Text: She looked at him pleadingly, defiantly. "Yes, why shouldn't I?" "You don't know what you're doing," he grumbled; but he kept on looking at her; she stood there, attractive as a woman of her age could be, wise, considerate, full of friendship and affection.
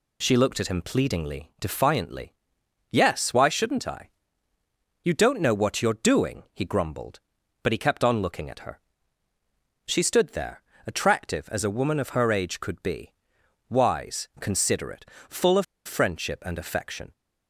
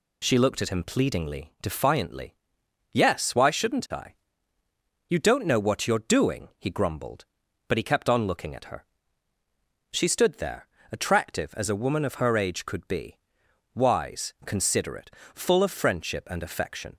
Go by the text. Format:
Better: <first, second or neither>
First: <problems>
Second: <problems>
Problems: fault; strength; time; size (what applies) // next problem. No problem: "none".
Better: second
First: pauses between "of" and "friendship"; slight; at 15.6 s; 0.21 s long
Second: none